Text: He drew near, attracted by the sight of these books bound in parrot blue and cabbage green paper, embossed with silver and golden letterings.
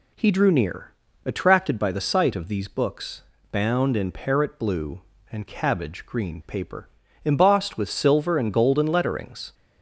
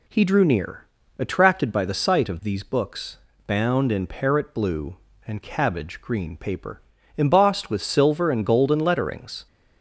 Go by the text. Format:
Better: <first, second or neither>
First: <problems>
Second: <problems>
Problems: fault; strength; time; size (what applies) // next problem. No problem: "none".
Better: neither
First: pauses between "books" and "bound"; slight; at 3.2 s; 0.28 s long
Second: pauses between "books" and "bound"; slight; at 3.1 s; 0.28 s long